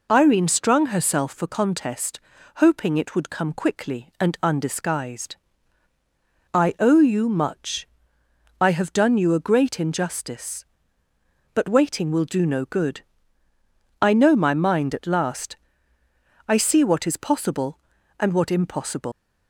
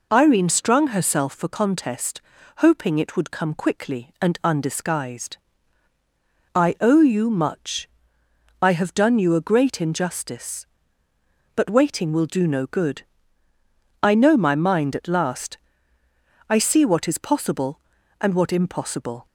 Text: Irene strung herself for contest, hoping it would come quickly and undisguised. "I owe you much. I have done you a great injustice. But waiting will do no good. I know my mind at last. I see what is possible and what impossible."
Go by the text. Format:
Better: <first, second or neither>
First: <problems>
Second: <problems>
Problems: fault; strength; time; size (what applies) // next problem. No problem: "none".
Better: second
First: leaves "impossible" unfinished; at 19.1 s; 125 ms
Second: none